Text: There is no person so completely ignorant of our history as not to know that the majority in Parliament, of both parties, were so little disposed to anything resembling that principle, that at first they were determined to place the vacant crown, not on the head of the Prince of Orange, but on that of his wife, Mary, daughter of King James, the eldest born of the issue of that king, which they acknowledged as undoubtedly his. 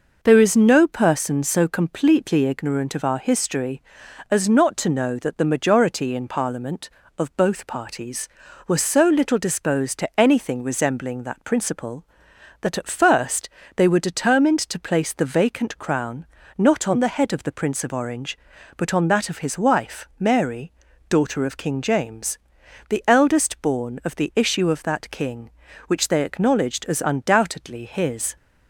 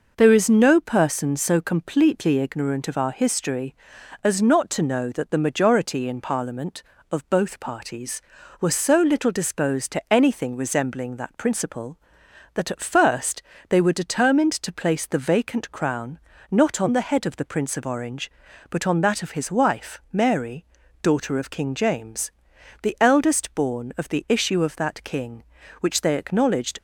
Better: first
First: pauses between "first" and "they"; slight; at 13.4 s; 0.28 s long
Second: pauses between "first" and "they"; slight; at 13.4 s; 0.28 s long // stops before "as undoubtedly his"; at 26.7 s

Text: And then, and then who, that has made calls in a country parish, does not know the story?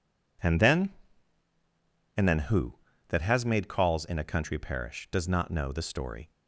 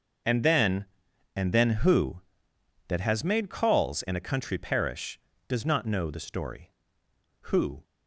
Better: first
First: none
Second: starts louder than the rest; noticeable; until 1.7 s; 6 dB // goes on to say "Who"; slight; from 7.4 s on; 0.36 s long

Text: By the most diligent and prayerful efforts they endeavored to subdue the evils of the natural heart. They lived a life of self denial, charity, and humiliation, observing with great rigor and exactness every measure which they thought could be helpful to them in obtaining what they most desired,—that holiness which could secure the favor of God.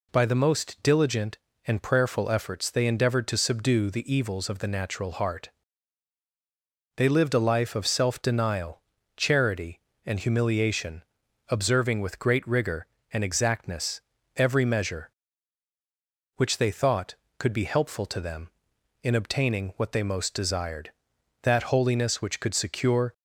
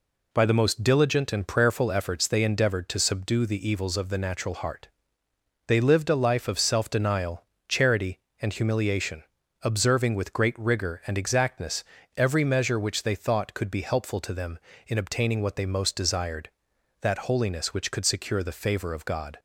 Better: second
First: pauses between "exactness" and "every"; slight; at 14.0 s; 0.34 s long // stops before "the favor of God"; at 23.1 s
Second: pauses between "exactness" and "every"; slight; at 11.8 s; 0.32 s long

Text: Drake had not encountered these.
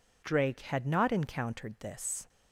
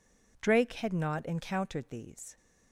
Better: second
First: says "this" for "these"; at 1.8 s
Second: none

